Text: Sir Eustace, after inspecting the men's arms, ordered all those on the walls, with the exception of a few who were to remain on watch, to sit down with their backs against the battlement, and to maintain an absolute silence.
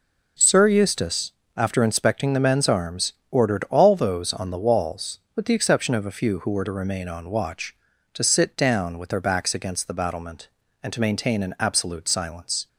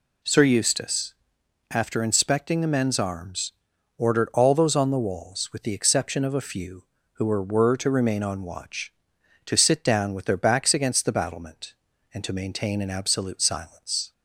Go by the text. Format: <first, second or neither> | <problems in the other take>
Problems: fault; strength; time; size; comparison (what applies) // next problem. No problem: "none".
first | says "were" twice; at 7.4 s